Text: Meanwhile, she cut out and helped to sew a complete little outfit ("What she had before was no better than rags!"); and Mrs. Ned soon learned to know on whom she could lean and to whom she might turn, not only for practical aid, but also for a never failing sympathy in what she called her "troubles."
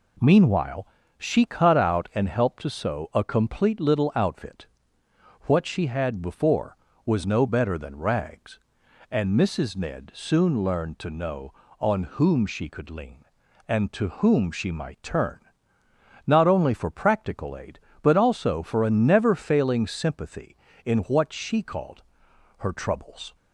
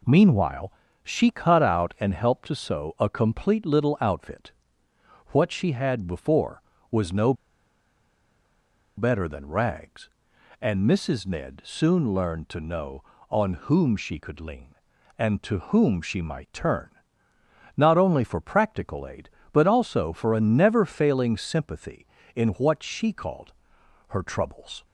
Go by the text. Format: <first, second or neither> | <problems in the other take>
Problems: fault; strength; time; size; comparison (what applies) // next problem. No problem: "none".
first | pauses between "no" and "better"; strong; at 7.3 s; 1.6 s long // pauses between "called" and "her"; noticeable; at 23.5 s; 0.56 s long; noticeable in the first